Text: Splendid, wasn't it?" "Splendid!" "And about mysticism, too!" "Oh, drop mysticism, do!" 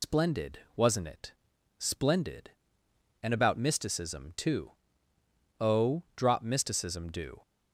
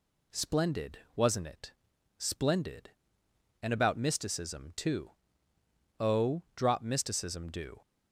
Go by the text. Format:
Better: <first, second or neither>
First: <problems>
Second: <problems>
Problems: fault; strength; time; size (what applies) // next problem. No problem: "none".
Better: second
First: loses the start of "Splendid"; at 0.0 s; 110 ms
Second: none